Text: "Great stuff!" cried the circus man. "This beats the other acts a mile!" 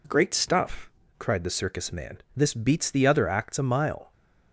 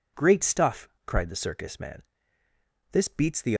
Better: first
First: none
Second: stops before "other acts a mile"; at 3.5 s

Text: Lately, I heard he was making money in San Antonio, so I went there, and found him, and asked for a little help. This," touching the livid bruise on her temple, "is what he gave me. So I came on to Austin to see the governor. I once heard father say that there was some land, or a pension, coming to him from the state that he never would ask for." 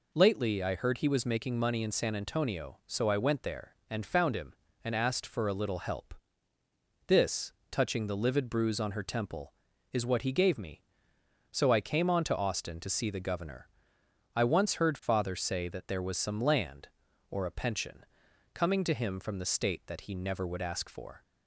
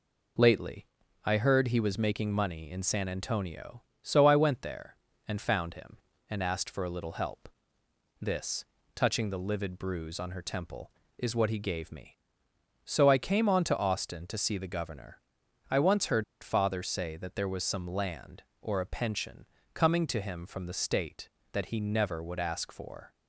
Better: first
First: none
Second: pauses between "heard" and "father"; slight; at 16.2 s; 0.19 s long

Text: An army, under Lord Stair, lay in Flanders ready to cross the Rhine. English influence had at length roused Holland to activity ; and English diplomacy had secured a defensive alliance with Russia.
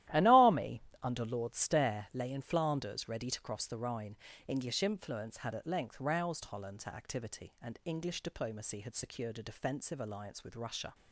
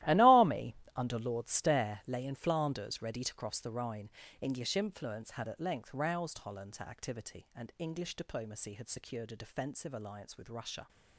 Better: first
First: starts louder than the rest; strong; until 1.3 s; 14 dB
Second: gets quieter; strong; throughout; 15 dB // starts louder than the rest; strong; until 1.2 s; 15.5 dB

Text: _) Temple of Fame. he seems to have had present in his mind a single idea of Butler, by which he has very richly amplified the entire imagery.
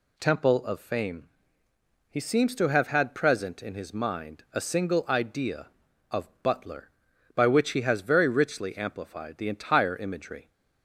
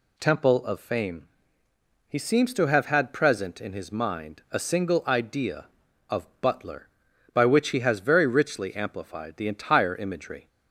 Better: neither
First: none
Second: none

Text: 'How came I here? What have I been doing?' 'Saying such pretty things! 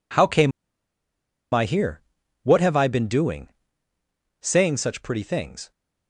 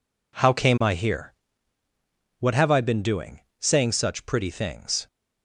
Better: second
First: pauses between "came" and "I"; at 0.5 s; 1.0 s long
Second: none

